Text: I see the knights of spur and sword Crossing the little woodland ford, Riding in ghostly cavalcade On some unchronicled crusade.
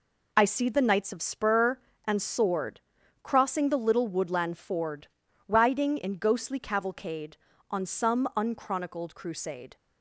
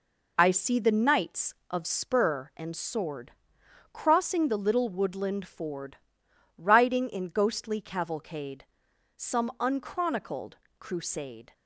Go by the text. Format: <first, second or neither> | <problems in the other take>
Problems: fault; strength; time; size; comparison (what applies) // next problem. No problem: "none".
first | pauses between "sword" and "Crossing"; noticeable; at 3.3 s; 0.60 s long; also in the first // skips "On"; at 8.8 s // pauses between "unchronicled" and "crusade"; slight; at 10.5 s; 0.26 s long